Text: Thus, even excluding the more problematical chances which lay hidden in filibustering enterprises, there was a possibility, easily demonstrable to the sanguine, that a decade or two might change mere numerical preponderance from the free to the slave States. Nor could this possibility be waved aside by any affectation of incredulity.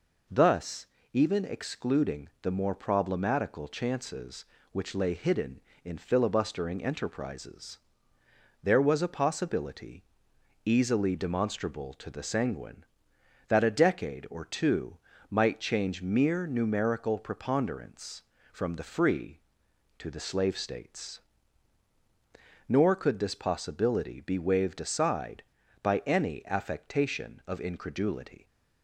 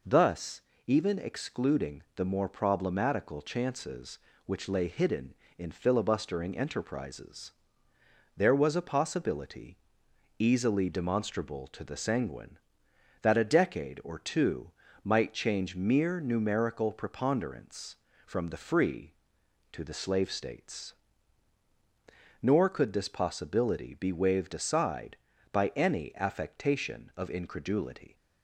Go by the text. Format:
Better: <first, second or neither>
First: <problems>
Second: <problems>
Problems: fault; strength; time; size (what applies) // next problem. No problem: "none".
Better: neither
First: pauses between "two" and "might"; slight; at 14.9 s; 0.32 s long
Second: pauses between "two" and "might"; slight; at 14.7 s; 0.32 s long